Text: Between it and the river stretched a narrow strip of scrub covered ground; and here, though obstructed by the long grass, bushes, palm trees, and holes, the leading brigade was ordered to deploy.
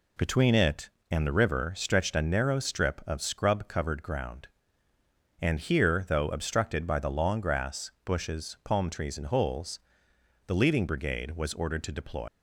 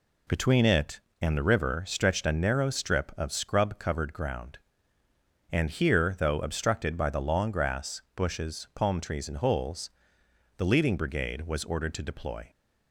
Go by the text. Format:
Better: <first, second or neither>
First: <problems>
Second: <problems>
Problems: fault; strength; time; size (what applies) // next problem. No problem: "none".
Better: second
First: leaves "deploy" unfinished; at 12.2 s; 115 ms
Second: none